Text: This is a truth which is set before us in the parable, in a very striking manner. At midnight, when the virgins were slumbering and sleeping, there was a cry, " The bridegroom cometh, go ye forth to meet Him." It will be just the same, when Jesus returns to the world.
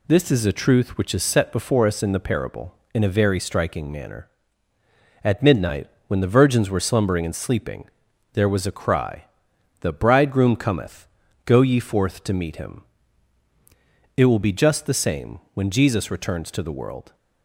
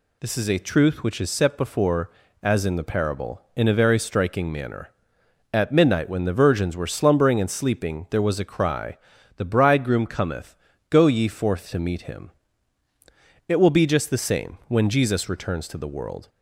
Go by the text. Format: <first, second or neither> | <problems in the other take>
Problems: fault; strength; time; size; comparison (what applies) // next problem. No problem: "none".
first | says "as" for "us"; at 2.4 s